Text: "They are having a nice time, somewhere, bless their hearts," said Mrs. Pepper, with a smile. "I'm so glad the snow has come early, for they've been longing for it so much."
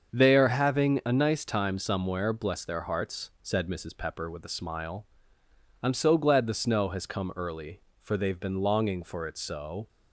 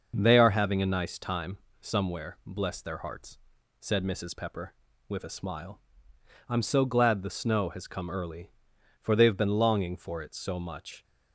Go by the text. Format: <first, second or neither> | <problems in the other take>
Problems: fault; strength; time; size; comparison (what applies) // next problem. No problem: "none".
second | starts louder than the rest; until 1.1 s; 6.5 dB; noticeable in the second // stops before "much"; at 9.8 s